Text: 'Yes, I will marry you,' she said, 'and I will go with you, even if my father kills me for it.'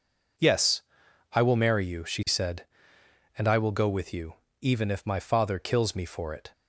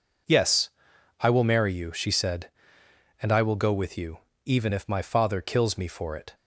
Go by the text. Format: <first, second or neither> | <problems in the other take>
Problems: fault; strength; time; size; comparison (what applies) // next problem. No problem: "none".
neither | none